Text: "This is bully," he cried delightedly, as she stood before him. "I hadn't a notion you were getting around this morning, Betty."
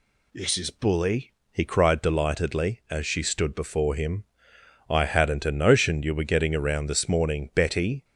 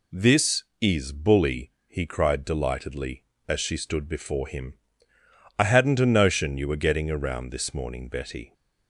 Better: neither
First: none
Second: none

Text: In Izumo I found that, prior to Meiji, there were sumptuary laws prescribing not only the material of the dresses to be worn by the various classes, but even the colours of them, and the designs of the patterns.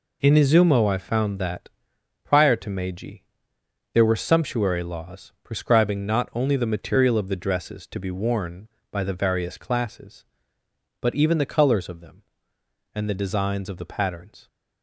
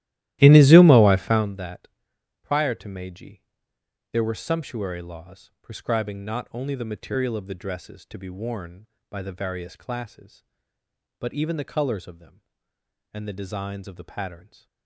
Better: first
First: none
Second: starts louder than the rest; strong; until 1.6 s; 15 dB

